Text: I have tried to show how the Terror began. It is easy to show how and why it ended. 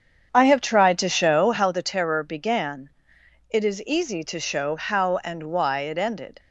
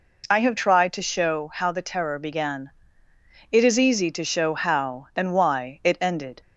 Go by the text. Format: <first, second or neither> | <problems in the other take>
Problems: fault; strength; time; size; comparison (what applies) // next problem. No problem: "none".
second | starts louder than the rest; strong; until 1.7 s; 7.5 dB